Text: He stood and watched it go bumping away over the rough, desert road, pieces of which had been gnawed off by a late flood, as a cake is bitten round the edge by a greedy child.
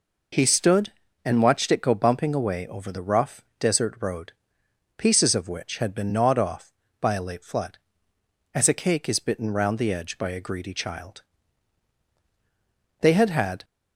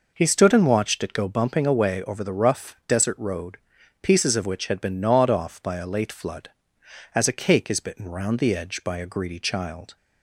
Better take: second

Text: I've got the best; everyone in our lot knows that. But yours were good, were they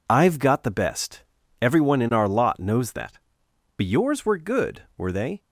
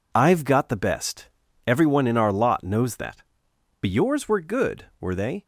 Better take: neither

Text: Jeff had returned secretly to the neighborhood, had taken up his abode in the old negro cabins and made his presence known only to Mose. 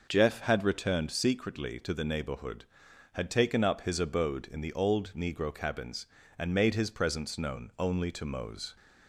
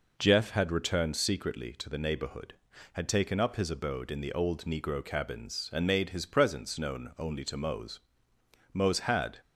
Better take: first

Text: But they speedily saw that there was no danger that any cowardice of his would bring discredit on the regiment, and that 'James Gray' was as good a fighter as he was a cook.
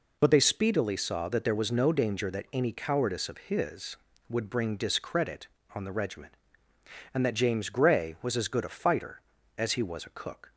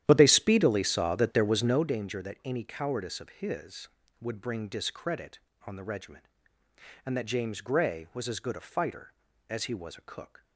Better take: first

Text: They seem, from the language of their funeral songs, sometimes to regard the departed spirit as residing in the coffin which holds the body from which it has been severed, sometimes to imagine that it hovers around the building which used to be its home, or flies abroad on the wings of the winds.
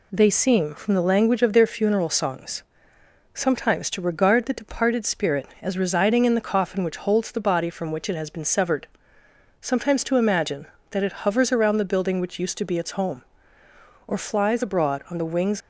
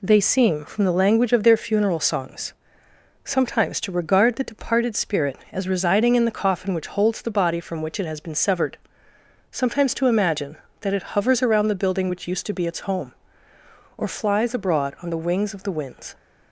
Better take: second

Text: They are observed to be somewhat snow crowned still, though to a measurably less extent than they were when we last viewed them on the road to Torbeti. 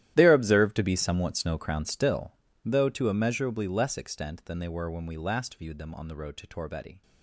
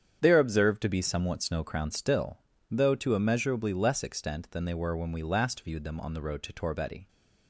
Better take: second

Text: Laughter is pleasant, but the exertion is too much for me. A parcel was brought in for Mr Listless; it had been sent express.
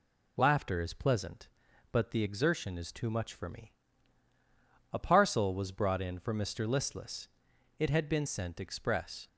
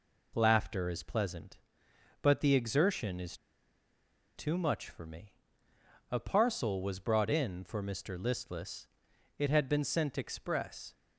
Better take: first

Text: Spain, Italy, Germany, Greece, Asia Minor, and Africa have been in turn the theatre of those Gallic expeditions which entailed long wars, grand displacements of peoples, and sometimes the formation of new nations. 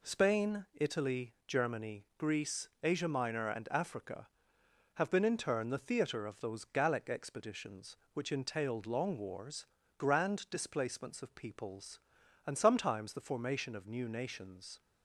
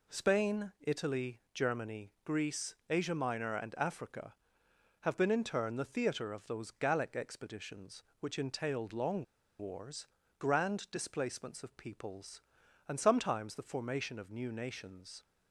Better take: first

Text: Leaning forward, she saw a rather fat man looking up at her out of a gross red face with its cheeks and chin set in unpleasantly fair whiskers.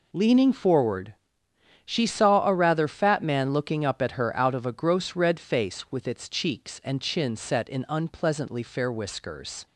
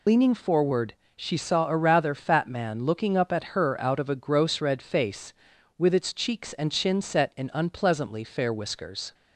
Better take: first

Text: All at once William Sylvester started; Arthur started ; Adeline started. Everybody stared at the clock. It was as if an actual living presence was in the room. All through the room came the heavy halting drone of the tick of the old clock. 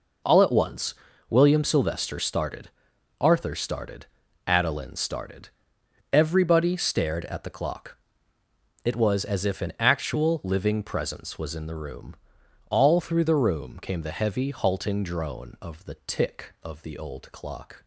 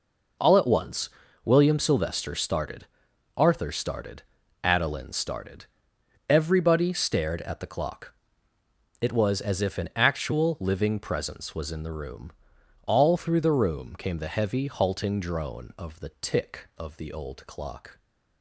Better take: neither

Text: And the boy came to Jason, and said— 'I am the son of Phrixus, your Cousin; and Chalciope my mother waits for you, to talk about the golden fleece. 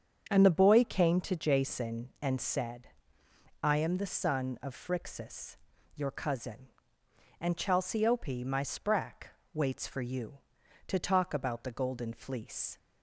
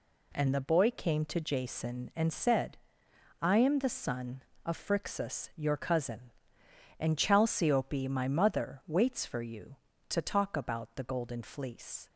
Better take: second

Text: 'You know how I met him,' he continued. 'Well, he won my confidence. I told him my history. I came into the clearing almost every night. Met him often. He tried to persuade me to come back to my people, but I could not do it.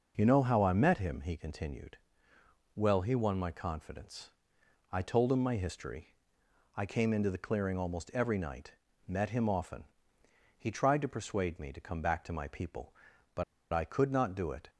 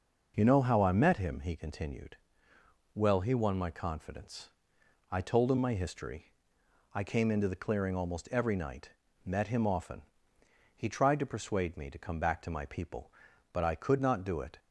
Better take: second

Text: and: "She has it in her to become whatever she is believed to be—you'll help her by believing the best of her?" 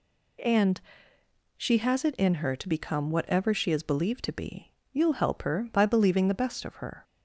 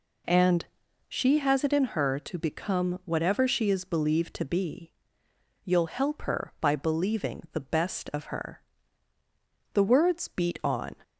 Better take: first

